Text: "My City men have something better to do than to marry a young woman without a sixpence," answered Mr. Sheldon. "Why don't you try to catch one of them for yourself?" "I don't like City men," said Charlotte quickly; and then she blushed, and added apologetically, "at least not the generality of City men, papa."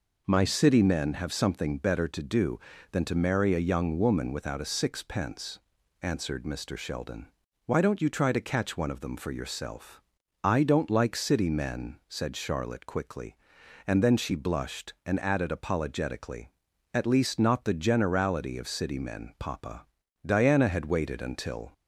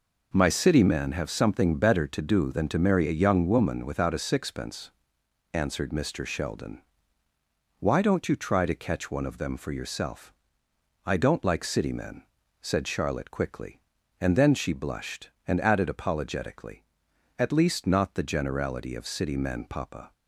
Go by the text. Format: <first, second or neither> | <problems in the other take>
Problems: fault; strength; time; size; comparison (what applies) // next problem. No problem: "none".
second | goes on to say "Diana had waited until"; from 20.2 s on; 1.4 s long